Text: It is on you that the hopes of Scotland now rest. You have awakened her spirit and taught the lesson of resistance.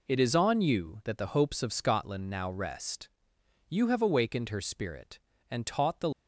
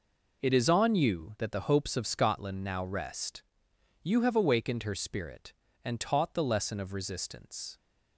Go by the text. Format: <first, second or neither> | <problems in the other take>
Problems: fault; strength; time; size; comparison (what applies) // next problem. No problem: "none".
second | stops before "lesson of resistance"; at 6.1 s